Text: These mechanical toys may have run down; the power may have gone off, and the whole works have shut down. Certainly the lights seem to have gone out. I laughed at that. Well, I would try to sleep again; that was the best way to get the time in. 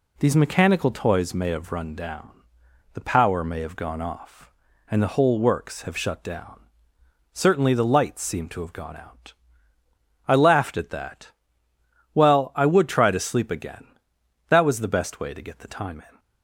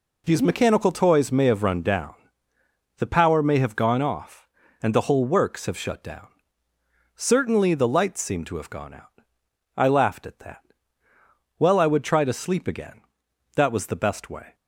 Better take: first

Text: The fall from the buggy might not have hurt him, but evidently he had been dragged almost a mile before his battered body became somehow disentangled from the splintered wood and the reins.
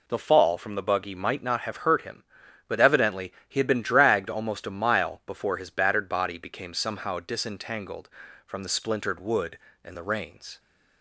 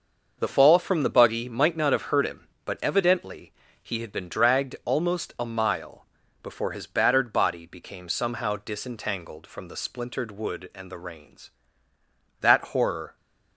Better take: first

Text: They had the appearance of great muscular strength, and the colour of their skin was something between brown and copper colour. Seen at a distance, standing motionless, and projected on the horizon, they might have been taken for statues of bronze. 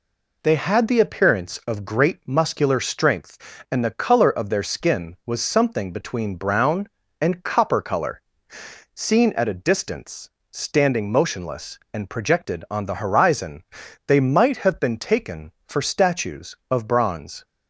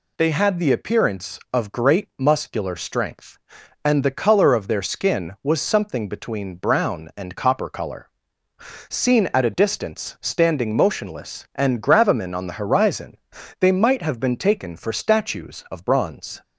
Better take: first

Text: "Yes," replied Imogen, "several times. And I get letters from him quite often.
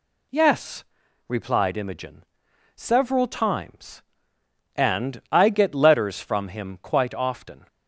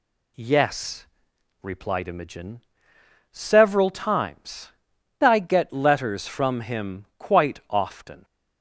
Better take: first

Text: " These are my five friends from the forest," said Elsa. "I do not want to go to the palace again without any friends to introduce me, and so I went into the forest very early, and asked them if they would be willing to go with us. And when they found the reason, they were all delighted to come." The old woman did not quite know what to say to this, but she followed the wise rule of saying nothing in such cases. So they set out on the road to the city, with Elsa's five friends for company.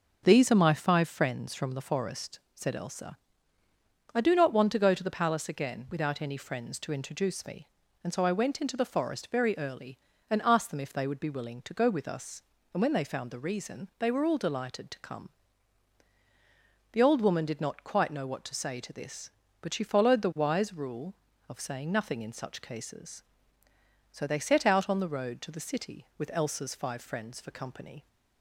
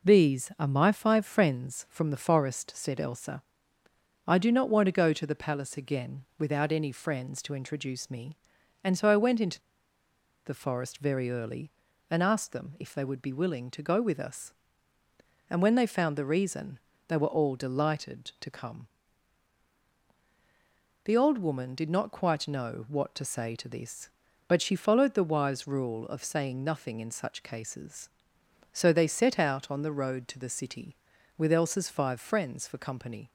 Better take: first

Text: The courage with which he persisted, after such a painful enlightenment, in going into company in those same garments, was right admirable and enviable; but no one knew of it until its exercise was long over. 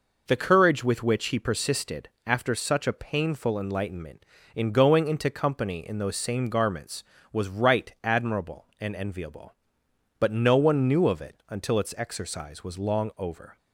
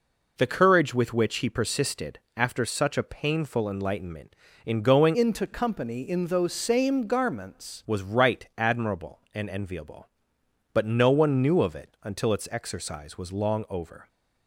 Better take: first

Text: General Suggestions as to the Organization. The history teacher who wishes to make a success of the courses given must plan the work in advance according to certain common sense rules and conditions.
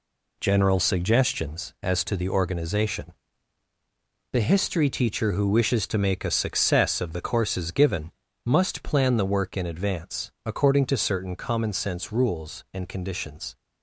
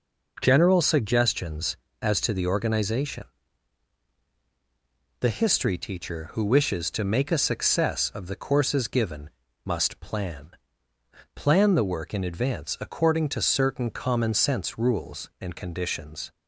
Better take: first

